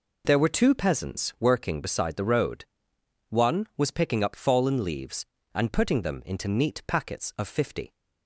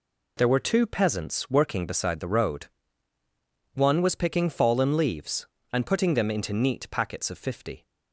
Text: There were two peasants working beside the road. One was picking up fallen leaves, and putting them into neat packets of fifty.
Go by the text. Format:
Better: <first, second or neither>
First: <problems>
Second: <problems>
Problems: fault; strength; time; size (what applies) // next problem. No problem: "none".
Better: first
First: none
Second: skips "up"; at 4.5 s